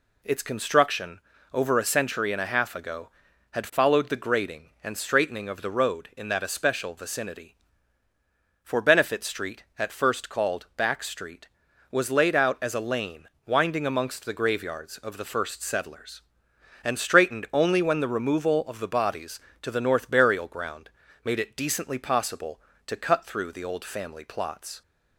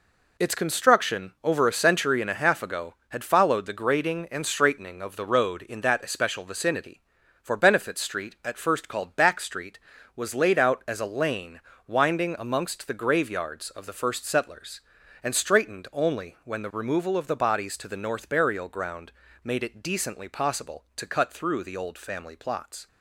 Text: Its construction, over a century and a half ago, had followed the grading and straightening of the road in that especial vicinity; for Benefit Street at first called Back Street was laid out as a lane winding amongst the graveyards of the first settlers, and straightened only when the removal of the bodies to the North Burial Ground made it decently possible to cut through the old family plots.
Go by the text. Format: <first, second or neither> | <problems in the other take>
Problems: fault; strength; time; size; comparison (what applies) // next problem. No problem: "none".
neither | pauses between "lane" and "winding"; slight; the same in both // pauses between "Ground" and "made"; slight; the same in both